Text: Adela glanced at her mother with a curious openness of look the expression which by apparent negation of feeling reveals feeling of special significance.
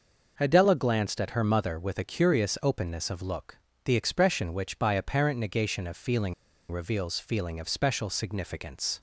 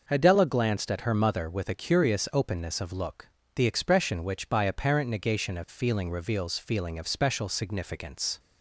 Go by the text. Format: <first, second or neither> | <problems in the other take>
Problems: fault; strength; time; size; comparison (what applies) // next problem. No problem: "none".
second | pauses between "look" and "the"; slight; at 3.5 s; 0.26 s long; slight in the second // pauses between "feeling" and "reveals"; at 6.3 s; 0.38 s long